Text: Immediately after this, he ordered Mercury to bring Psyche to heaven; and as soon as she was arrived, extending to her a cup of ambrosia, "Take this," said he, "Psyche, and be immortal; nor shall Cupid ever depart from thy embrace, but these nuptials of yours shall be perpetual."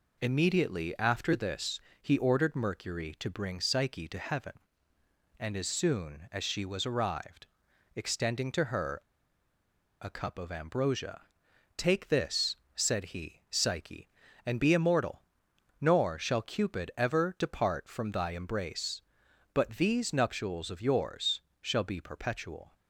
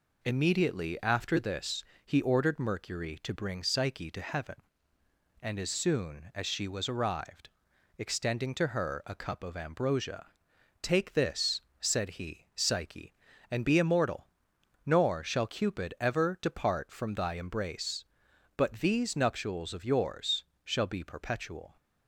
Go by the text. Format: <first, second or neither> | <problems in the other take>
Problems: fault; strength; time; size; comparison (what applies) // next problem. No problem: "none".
second | pauses between "her" and "a"; at 8.9 s; 1.0 s long // pauses between "yours" and "shall"; slight; at 21.3 s; 0.22 s long; slight in the second